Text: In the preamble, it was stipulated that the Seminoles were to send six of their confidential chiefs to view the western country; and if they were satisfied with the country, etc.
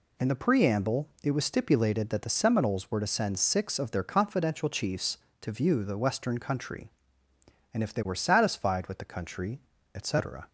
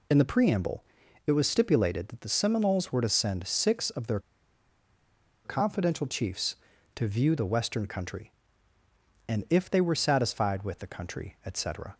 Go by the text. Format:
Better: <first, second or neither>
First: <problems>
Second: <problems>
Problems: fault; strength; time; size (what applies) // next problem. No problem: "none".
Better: first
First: none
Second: pauses between "their" and "confidential"; at 4.2 s; 1.2 s long